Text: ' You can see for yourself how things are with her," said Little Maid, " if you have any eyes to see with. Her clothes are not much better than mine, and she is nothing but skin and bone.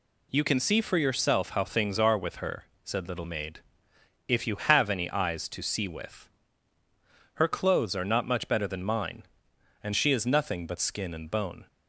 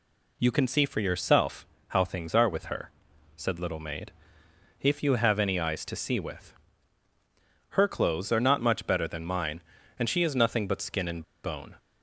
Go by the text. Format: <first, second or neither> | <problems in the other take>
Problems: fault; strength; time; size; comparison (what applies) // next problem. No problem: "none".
first | pauses between "yourself" and "how"; slight; at 1.6 s; 0.24 s long // pauses between "and" and "bone"; slight; at 11.2 s; 0.21 s long